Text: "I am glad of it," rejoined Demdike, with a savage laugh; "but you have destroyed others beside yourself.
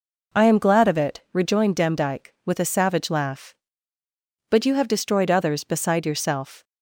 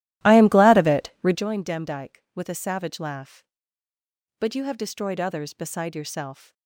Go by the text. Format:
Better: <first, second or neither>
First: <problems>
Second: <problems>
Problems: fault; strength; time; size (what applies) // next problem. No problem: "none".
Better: first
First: none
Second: starts louder than the rest; strong; until 1.4 s; 14.5 dB